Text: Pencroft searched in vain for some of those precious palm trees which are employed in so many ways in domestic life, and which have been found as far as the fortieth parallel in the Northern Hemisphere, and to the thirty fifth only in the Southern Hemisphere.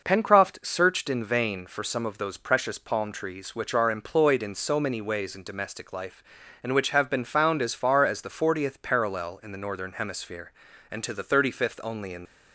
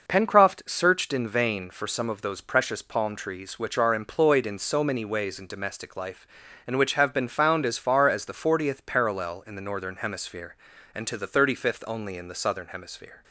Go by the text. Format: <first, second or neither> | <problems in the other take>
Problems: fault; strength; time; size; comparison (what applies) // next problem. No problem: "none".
second | stops before "the Southern Hemisphere"; at 12.2 s